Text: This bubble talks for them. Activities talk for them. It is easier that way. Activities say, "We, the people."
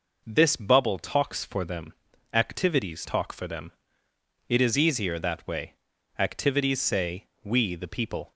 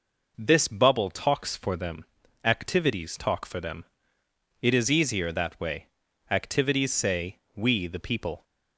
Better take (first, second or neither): neither